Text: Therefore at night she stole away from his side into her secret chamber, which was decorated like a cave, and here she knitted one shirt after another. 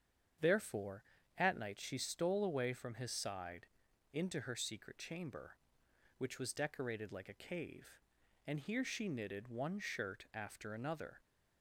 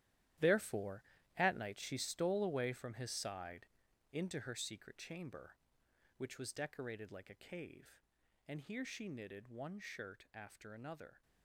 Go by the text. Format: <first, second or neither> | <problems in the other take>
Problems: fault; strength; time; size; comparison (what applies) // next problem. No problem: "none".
first | gets quieter; strong; throughout; 13.5 dB // starts louder than the rest; strong; until 1.7 s; 12.5 dB; strong in the first // pauses between "side" and "into"; noticeable; at 3.6 s; 0.48 s long; noticeable in the first